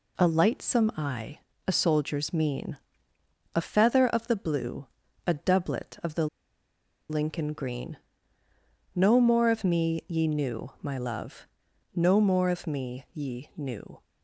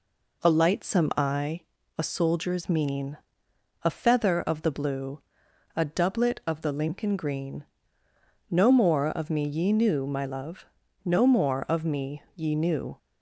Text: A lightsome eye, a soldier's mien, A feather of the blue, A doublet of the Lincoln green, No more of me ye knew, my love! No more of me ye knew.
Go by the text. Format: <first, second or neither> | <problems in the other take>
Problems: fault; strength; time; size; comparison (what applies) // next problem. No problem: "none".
second | pauses between "the" and "Lincoln"; noticeable; at 6.2 s; 0.83 s long